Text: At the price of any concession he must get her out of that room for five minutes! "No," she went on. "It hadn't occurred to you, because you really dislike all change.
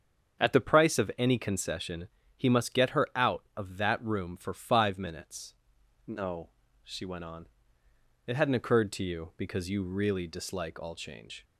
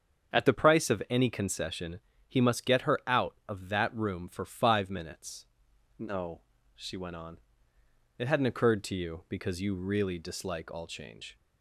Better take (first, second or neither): neither